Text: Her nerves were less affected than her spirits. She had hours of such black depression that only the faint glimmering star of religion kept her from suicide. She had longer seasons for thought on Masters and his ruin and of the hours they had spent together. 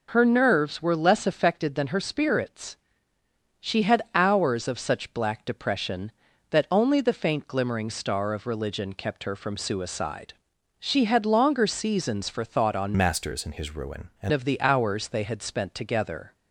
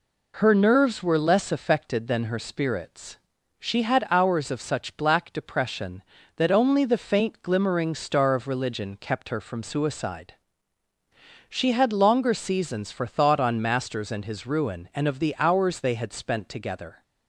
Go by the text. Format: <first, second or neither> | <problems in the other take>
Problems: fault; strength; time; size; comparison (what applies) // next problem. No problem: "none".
second | changes voice from "Masters" to "and"; from 12.9 to 14.3 s; 1.4 s long